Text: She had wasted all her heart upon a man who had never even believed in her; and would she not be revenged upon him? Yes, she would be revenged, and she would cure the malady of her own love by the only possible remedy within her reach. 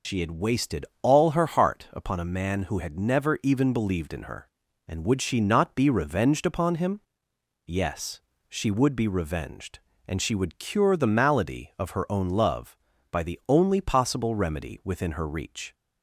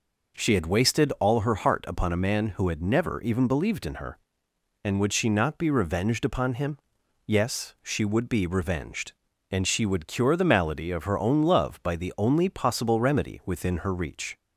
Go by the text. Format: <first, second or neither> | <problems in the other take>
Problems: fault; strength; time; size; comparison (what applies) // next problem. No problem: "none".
second | loses the start of "She"; at 0.0 s; 70 ms // pauses between "wasted" and "all"; slight; at 0.8 s; 0.16 s long